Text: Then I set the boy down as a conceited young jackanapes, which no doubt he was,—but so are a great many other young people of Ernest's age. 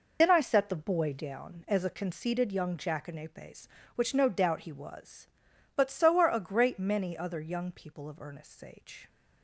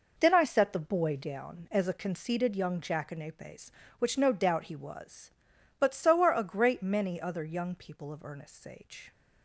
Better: second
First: loses the start of "Then"; at 0.2 s; 55 ms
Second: none

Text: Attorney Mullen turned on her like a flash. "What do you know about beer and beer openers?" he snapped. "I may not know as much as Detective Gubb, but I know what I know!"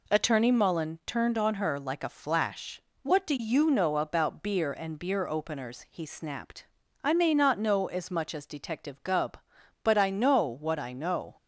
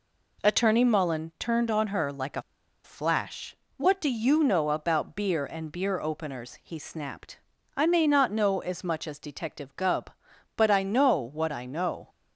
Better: first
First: none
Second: pauses between "a" and "flash"; at 2.4 s; 0.42 s long

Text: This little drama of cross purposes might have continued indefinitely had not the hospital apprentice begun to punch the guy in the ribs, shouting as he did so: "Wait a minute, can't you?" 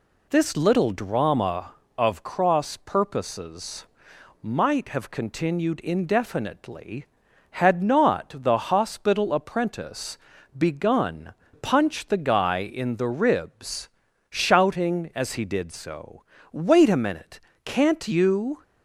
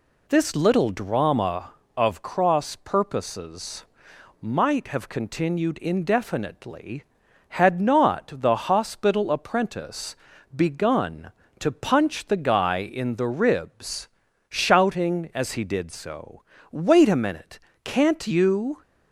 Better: second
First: pauses between "purposes" and "might"; noticeable; at 3.8 s; 0.56 s long // pauses between "apprentice" and "begun"; at 10.1 s; 0.40 s long // skips "to"; at 11.4 s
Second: pauses between "purposes" and "might"; noticeable; at 3.8 s; 0.56 s long // pauses between "apprentice" and "begun"; at 10.1 s; 0.40 s long

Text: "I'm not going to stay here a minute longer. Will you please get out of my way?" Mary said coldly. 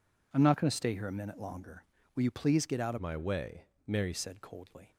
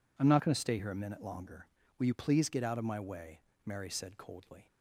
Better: second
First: changes voice from "my" to "Mary"; from 2.9 to 4.1 s; 1.2 s long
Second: none

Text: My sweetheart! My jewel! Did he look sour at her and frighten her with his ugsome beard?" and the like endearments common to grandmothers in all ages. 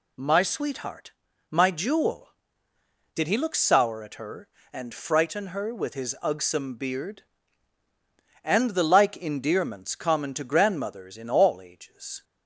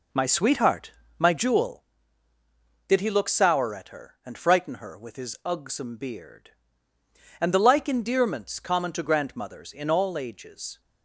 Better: first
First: none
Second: starts louder than the rest; noticeable; until 1.9 s; 4.5 dB

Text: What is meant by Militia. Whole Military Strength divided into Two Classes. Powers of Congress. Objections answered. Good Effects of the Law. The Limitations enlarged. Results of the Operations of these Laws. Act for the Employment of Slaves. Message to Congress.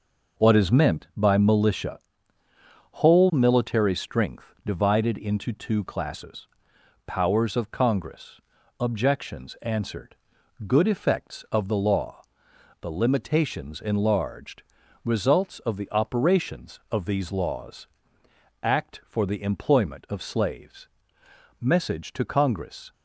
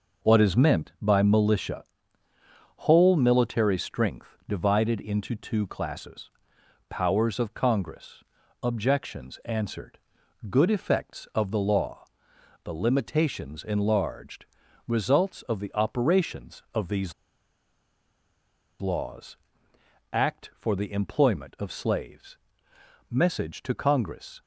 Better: first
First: none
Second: pauses between "these" and "Laws"; strong; at 17.1 s; 1.6 s long

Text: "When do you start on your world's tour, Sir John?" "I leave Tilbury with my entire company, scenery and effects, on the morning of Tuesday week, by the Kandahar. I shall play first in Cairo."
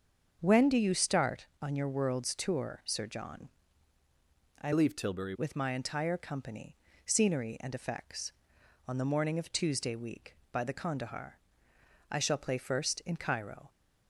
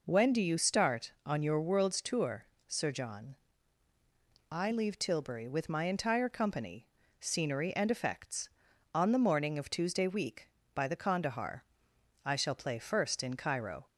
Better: second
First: starts louder than the rest; until 1.4 s; 7 dB // changes voice from "leave" to "Tilbury"; from 4.7 to 5.3 s; 0.6 s long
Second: none

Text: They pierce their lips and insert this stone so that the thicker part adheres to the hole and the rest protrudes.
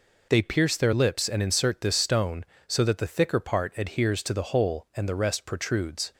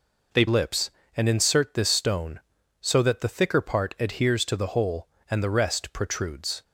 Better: first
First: none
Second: skips "pierce their"; at 0.4 s

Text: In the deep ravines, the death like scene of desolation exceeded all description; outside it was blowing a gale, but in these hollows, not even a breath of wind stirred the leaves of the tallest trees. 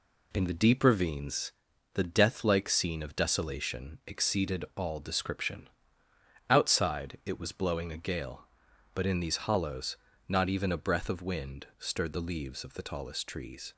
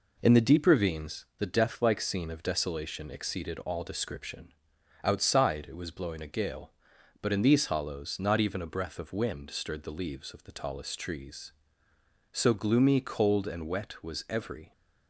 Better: first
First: none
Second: goes on to say "So gloomy cold and wet was every"; strong; from 12.3 s on; 2.4 s long

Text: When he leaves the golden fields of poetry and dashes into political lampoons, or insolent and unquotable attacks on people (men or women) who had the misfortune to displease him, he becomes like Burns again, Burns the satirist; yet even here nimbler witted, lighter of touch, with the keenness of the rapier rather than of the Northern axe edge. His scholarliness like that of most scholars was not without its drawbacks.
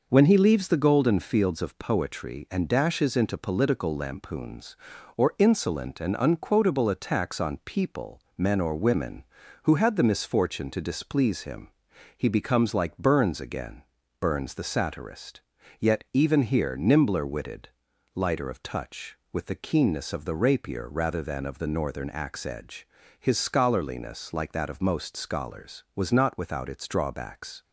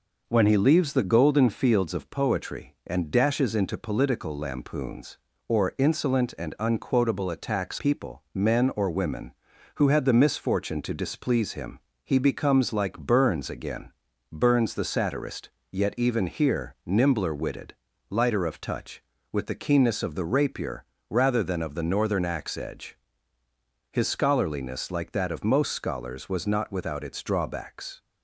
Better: first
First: none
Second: skips "on"; at 7.7 s // pauses between "rapier" and "rather"; slight; at 20.8 s; 0.26 s long

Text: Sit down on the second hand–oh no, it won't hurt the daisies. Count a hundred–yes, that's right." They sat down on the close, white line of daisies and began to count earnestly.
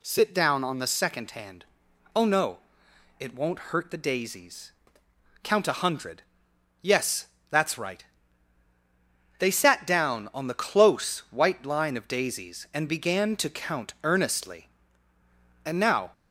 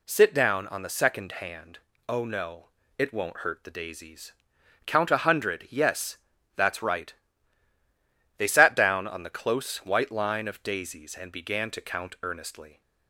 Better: second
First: goes on to say "And now"; slight; from 15.6 s on; 0.48 s long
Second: none

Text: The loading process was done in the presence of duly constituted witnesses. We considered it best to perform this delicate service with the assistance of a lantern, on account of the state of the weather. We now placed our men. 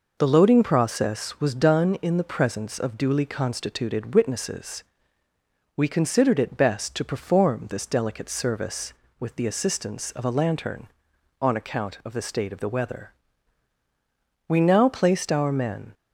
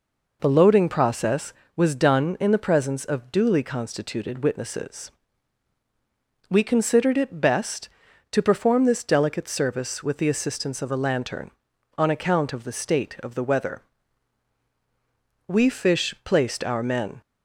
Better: first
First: none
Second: says "fish" for "now"; at 15.6 s

